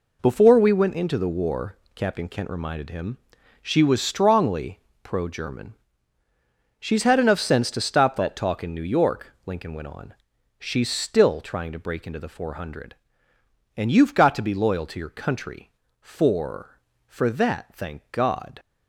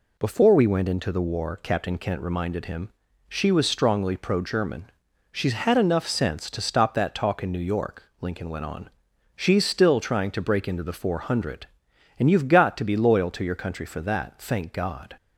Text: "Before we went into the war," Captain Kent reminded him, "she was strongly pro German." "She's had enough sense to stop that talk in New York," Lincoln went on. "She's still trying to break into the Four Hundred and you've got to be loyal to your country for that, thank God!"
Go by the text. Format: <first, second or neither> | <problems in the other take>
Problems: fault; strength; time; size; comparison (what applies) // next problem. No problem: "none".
second | pauses between "strongly" and "pro"; slight; at 4.8 s; 0.20 s long // says "for" twice; at 17.0 s